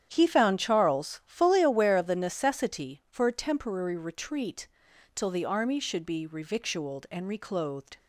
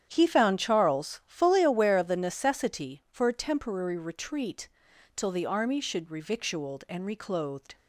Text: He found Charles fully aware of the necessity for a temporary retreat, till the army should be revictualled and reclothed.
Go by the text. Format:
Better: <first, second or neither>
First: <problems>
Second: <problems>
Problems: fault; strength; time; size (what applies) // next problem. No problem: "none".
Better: first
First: starts louder than the rest; strong; until 1.1 s; 9.5 dB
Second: starts louder than the rest; strong; until 1.1 s; 9.5 dB // skips "be"; at 6.0 s